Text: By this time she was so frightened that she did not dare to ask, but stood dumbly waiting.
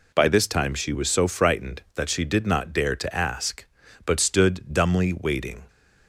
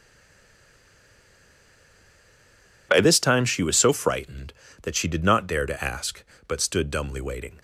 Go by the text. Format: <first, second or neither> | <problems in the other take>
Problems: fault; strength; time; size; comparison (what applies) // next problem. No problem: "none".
first | stays silent before the first word; strong; until 2.8 s; 2.8 s long